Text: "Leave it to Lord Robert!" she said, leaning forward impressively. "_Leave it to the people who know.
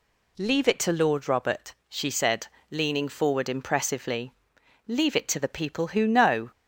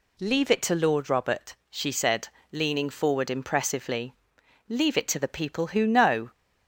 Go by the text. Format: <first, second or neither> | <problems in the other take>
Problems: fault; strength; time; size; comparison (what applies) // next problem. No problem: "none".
neither | none